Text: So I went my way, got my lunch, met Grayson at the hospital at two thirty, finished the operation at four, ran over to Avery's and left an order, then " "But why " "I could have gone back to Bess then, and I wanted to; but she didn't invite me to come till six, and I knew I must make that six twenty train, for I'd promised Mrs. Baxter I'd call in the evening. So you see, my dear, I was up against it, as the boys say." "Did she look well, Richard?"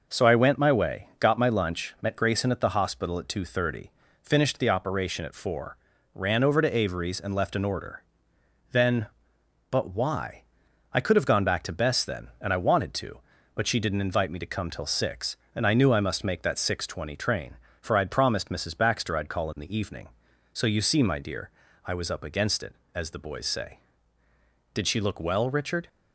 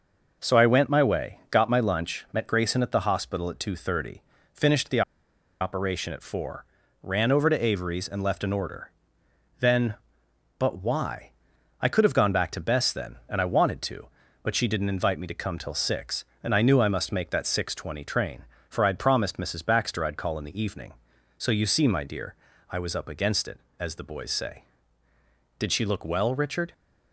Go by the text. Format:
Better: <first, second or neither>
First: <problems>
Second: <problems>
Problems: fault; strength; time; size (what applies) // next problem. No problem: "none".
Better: first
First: none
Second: pauses between "the" and "operation"; noticeable; at 5.0 s; 0.59 s long